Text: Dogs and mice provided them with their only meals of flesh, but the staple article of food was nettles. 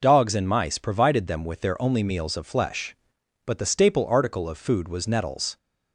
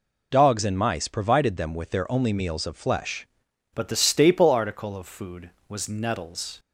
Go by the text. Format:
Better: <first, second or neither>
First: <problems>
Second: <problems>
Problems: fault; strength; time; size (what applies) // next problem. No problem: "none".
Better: first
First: none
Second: changes voice at "but"; from 3.7 s on; 2.8 s long